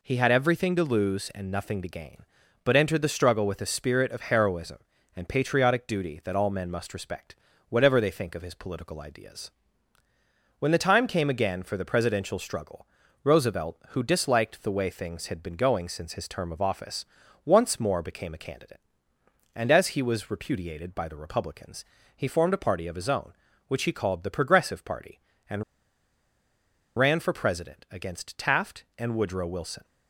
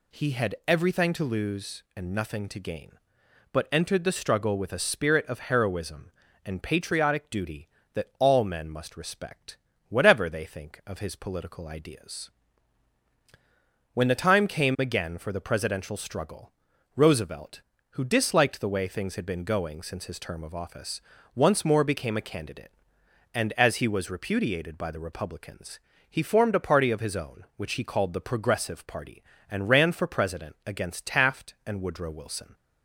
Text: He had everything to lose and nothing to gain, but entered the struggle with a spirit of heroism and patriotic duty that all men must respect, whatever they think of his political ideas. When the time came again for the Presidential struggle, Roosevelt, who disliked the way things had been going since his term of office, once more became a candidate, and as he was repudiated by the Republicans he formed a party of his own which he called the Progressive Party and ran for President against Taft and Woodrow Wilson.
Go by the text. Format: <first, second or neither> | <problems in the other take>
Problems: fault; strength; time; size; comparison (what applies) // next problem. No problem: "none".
second | pauses between "Republicans" and "he"; slight; at 21.8 s; 0.32 s long; slight in the second // pauses between "and" and "ran"; strong; at 25.6 s; 1.3 s long